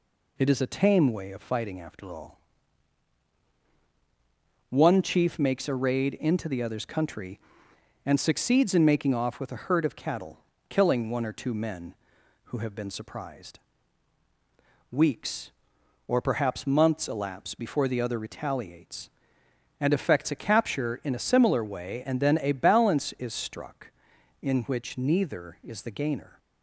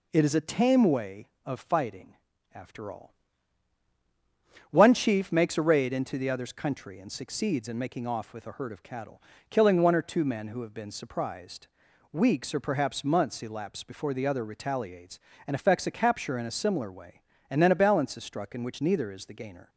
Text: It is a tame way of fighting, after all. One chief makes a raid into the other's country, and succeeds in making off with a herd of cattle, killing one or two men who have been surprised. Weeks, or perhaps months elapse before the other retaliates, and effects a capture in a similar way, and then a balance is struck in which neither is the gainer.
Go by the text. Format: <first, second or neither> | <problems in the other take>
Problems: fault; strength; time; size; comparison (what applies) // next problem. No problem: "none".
neither | none